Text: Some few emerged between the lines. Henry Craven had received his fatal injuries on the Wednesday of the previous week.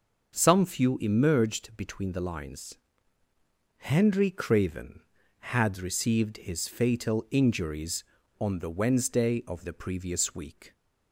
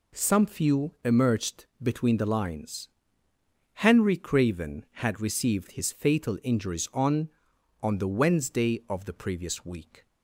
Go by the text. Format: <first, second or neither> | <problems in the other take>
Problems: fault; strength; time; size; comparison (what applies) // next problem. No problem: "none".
first | pauses between "emerged" and "between"; slight; at 1.6 s; 0.16 s long // says "on" twice; at 7.8 s